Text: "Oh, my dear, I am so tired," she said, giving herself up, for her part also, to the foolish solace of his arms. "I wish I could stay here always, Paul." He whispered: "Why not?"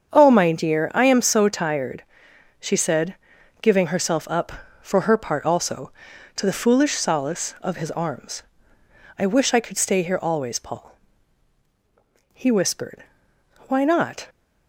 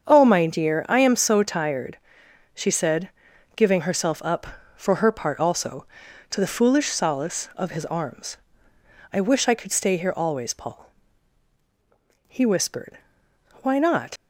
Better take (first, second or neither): first